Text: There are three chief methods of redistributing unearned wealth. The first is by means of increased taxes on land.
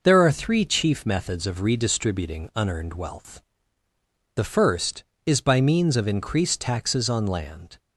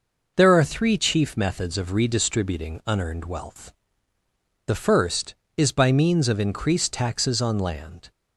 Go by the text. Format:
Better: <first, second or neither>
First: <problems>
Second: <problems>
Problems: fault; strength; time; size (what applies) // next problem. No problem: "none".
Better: neither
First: none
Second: none